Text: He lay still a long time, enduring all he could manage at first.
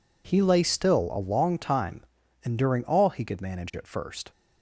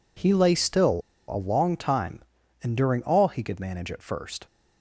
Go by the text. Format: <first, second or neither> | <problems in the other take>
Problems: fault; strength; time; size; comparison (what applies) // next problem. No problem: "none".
first | pauses between "still" and "a"; slight; at 1.0 s; 0.28 s long